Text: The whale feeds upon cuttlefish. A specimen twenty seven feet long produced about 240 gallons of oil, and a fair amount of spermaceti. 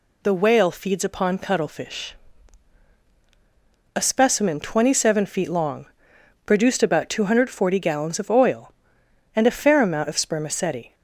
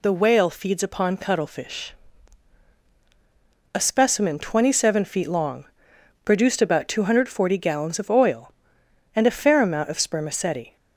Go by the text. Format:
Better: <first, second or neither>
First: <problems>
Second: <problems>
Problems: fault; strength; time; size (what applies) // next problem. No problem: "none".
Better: neither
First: pauses between "long" and "produced"; noticeable; at 5.8 s; 0.60 s long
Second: pauses between "long" and "produced"; noticeable; at 5.6 s; 0.60 s long